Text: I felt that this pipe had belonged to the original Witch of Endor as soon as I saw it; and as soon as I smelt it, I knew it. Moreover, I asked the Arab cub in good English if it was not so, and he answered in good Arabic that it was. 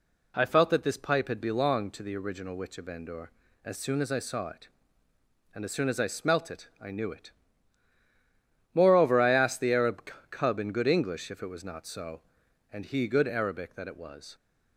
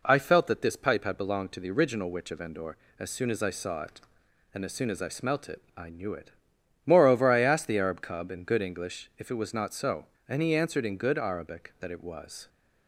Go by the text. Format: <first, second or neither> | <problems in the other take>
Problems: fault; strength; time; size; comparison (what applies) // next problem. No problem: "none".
second | pauses between "Arab" and "cub"; slight; at 10.1 s; 0.20 s long // skips "answered in"; at 13.0 s